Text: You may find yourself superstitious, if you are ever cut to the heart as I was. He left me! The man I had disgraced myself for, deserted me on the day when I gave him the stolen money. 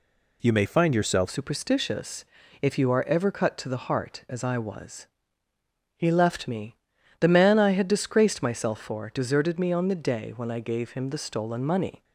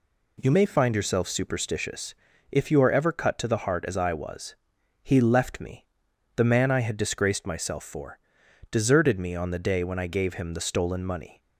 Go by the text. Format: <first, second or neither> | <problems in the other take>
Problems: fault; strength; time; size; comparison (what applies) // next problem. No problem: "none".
second | changes voice at "superstitious"; from 1.2 s on; 10.8 s long